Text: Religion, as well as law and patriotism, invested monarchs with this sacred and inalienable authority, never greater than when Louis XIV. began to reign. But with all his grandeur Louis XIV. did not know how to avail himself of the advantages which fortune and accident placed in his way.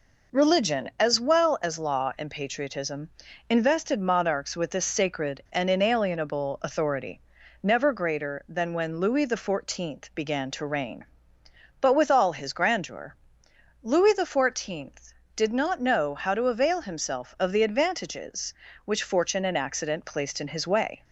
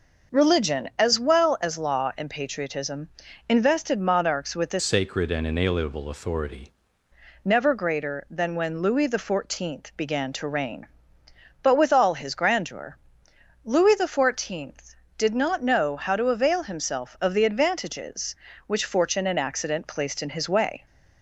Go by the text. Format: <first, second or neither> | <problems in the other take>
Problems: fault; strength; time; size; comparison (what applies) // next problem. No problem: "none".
first | changes voice from "sacred" to "authority"; from 4.8 to 6.7 s; 1.9 s long // pauses between "grandeur" and "Louis"; noticeable; at 12.9 s; 0.70 s long; noticeable in the first